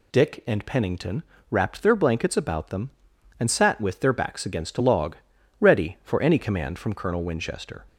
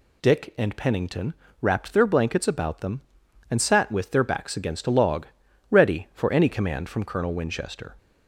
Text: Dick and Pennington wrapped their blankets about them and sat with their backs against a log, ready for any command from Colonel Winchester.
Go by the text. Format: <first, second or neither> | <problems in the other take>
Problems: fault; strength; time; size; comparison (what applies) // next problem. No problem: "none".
neither | pauses between "Pennington" and "wrapped"; slight; the same in both